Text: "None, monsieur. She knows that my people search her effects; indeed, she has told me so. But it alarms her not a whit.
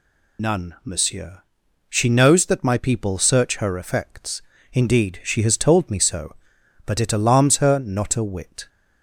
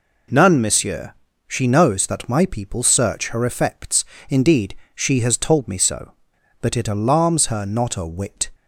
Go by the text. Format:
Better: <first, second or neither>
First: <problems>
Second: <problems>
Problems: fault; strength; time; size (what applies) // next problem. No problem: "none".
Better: second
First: loses the start of "None"; at 0.3 s; 70 ms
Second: none